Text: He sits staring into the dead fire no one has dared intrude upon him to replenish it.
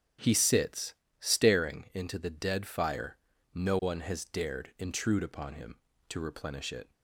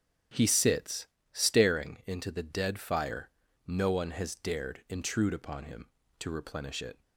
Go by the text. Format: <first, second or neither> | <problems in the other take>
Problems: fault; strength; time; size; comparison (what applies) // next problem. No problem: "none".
neither | starts louder than the rest; strong; the same in both // pauses between "sits" and "staring"; slight; the same in both // pauses between "fire" and "no"; the same in both